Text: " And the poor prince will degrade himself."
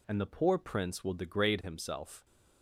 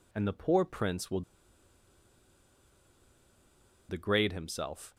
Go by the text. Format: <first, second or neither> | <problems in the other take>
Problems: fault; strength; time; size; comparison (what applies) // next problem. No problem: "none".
first | pauses between "will" and "degrade"; strong; at 1.2 s; 2.6 s long